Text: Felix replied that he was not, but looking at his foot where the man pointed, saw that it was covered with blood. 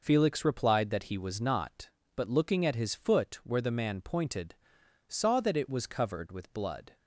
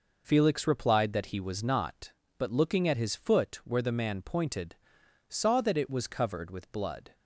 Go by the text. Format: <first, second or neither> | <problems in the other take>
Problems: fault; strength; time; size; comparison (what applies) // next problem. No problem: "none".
neither | none